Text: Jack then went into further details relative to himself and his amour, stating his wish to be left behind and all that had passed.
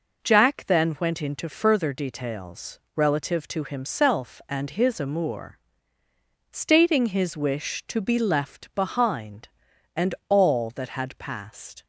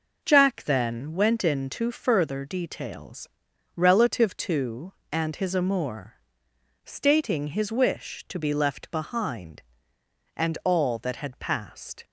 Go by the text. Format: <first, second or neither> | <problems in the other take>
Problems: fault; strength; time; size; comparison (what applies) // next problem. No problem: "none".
first | pauses between "details" and "relative"; noticeable; at 3.2 s; 0.46 s long; slight in the first // skips "himself"; at 5.0 s